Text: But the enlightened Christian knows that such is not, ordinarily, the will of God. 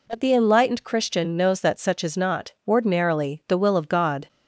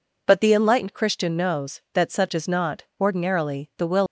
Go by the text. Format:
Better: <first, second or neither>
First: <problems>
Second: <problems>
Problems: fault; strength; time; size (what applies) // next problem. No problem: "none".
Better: first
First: none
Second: stops before "of God"; at 4.0 s